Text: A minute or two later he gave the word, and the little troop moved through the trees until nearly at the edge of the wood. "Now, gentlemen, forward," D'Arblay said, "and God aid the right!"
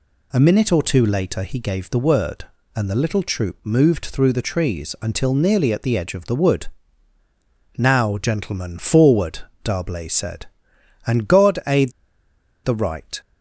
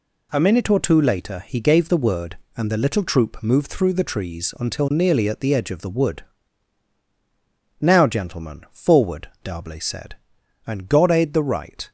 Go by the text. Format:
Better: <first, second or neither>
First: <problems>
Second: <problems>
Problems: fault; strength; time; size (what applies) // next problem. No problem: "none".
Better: second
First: pauses between "aid" and "the"; noticeable; at 11.9 s; 0.74 s long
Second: none